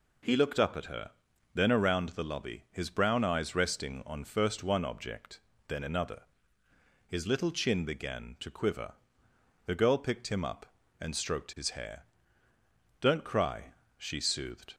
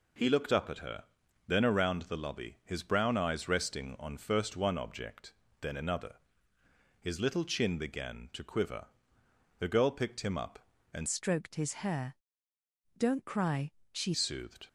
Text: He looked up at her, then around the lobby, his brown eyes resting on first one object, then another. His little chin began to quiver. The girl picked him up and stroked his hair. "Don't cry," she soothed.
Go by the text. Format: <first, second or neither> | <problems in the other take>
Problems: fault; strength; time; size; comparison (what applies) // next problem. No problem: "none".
first | changes voice from "stroked" to "she"; from 11.0 to 14.1 s; 3.1 s long